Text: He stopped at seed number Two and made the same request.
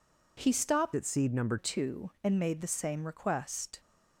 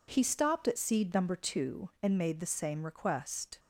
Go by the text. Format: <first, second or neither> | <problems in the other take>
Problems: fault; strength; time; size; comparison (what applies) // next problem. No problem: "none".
second | changes voice from "at" to "number"; from 0.9 to 1.5 s; 0.6 s long